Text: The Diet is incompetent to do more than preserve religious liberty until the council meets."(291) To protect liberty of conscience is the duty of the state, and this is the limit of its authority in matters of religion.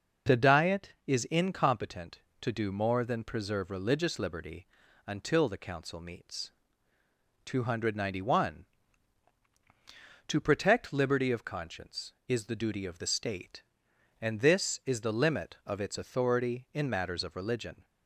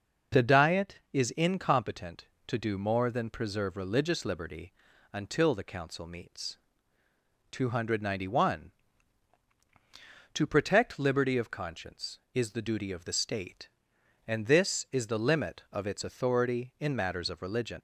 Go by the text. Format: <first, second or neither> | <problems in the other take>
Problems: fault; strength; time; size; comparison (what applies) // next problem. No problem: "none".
first | starts louder than the rest; until 1.5 s; 6.5 dB; also in the first // pauses between "liberty" and "until"; at 4.7 s; 0.40 s long; also in the first // leaves "religion" unfinished; at 17.7 s; 105 ms